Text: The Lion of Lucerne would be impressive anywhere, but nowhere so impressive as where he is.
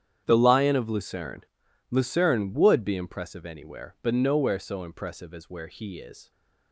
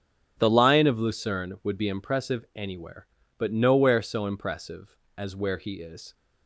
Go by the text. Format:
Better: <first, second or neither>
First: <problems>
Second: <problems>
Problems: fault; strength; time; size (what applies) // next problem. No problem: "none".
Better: second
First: starts louder than the rest; strong; until 1.2 s; 9 dB // says "Lucerne" twice; at 1.9 s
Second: starts louder than the rest; strong; until 1.4 s; 9 dB